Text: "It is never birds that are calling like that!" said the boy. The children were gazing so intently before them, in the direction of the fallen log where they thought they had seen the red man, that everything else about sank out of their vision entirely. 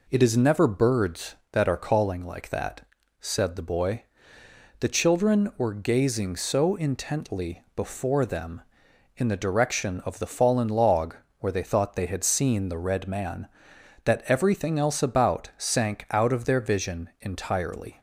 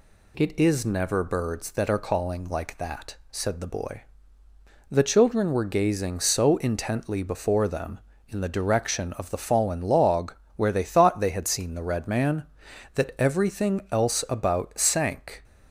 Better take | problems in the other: first | pauses between "log" and "where"; slight; at 10.3 s; 0.24 s long; slight in the first // stops before "out of their vision entirely"; at 15.4 s

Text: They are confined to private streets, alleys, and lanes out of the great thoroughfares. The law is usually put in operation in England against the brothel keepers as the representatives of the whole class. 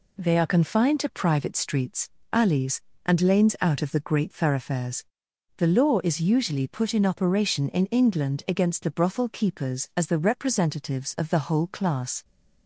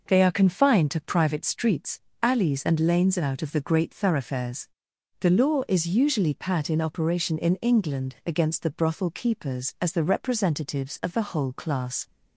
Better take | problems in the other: first | says "pat" for "put"; at 6.3 s

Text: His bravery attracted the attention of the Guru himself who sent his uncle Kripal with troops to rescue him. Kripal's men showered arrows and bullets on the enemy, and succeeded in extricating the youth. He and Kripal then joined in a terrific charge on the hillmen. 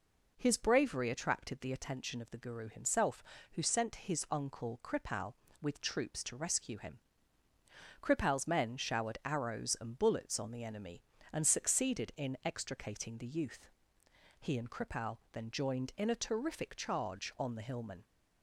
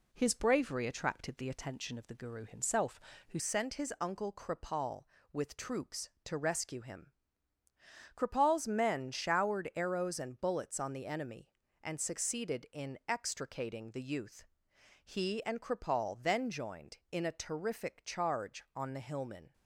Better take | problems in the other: first | changes voice at "sent"; from 3.3 s on; 16.2 s long

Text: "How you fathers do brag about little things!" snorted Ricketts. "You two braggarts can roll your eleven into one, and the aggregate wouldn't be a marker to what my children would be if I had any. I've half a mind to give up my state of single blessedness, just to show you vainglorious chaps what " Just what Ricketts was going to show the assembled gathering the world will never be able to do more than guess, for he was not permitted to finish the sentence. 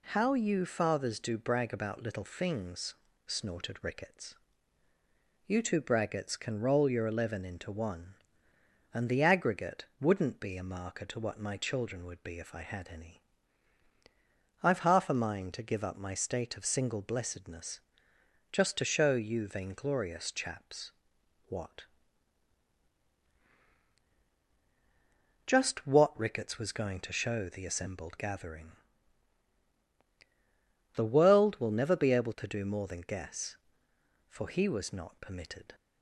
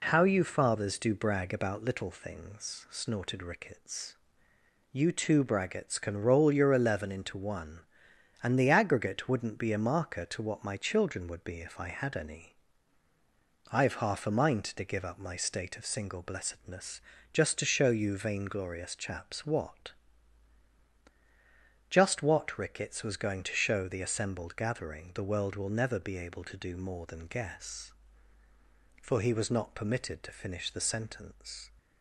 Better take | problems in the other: second | pauses between "chaps" and "what"; noticeable; at 20.9 s; 0.56 s long // pauses between "gathering" and "the"; strong; at 28.7 s; 2.2 s long // stops before "to finish the sentence"; at 35.7 s

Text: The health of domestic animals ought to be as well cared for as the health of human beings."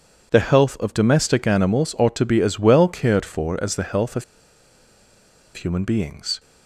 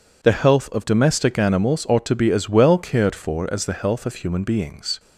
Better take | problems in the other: second | pauses between "of" and "human"; strong; at 4.2 s; 1.3 s long

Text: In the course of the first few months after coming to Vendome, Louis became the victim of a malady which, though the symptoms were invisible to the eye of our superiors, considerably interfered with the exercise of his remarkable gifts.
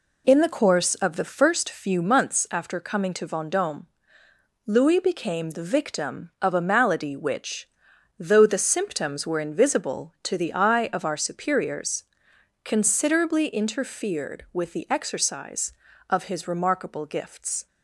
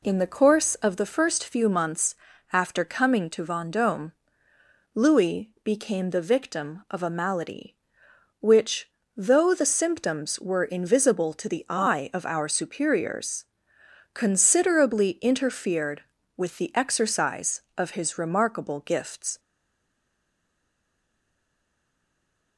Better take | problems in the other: first | pauses between "months" and "after"; slight; at 2.1 s; 0.36 s long // stays silent after the last word; strong; from 19.3 s on; 3.2 s long

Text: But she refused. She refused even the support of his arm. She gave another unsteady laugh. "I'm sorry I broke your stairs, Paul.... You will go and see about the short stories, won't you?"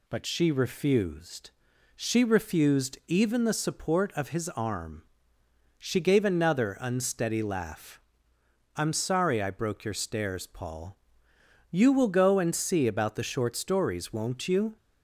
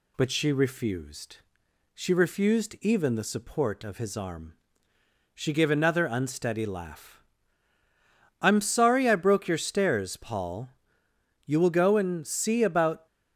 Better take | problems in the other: first | stops before "the short stories won't you"; at 13.0 s

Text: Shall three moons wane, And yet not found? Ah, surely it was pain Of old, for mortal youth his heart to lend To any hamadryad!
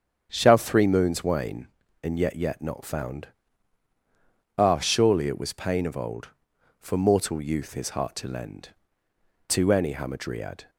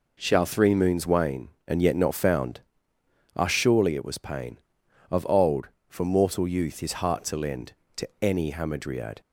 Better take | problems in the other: second | starts louder than the rest; strong; until 1.3 s; 7.5 dB // says "yet" twice; at 2.3 s

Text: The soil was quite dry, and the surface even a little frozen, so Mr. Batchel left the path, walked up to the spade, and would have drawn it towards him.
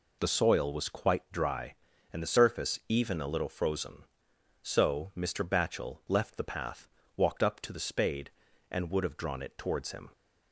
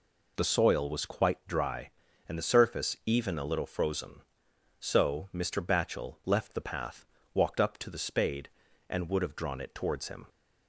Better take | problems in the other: neither | none

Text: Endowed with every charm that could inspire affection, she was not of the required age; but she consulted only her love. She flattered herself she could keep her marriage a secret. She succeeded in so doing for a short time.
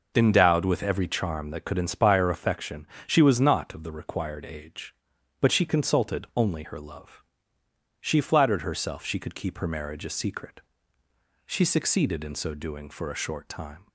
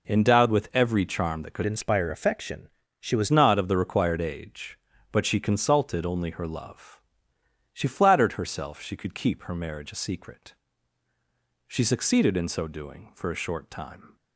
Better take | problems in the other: first | changes voice from "inspire" to "was"; from 1.6 to 3.3 s; 1.7 s long

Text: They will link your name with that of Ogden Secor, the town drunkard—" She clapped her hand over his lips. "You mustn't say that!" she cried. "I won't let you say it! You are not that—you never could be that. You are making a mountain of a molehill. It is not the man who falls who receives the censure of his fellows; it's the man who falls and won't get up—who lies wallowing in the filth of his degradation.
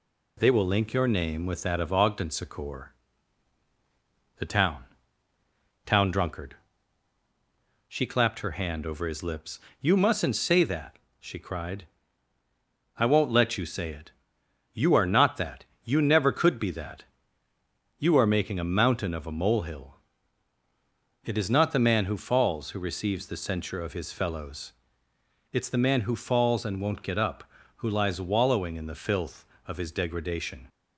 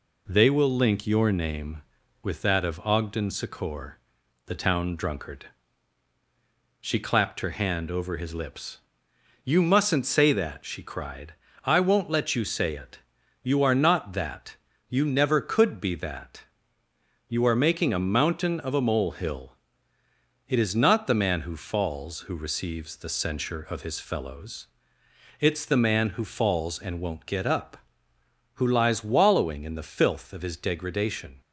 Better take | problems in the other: second | says "town" twice; at 5.8 s

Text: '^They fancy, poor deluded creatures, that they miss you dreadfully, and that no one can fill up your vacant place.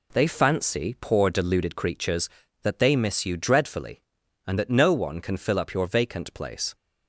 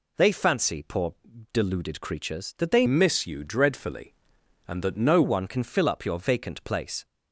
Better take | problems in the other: first | pauses between "poor" and "deluded"; at 1.1 s; 0.38 s long // changes voice from "miss" to "no"; from 2.8 to 5.2 s; 2.4 s long

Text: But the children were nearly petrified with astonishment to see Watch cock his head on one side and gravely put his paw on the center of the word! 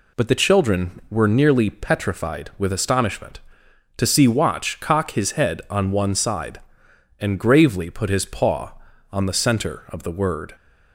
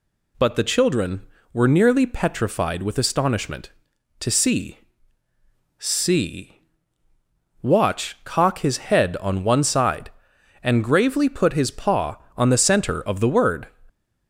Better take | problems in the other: first | says "see" twice; at 5.7 s

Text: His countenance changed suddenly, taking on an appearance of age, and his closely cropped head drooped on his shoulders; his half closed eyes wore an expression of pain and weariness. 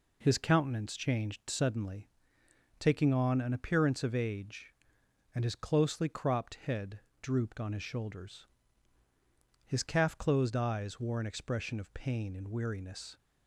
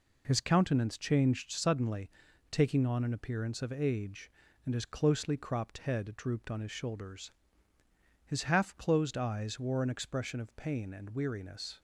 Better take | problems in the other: second | pauses between "head" and "drooped"; slight; at 6.9 s; 0.22 s long // says "calf" for "half"; at 9.8 s

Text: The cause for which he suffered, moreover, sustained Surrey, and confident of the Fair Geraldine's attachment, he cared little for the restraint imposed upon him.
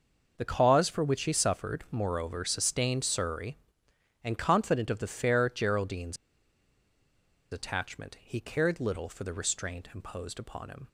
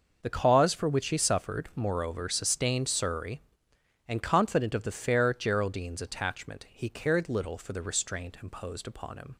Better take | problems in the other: second | starts louder than the rest; noticeable; until 1.3 s; 6 dB; noticeable in the second // pauses between "Geraldine's" and "attachment"; strong; at 6.1 s; 1.3 s long

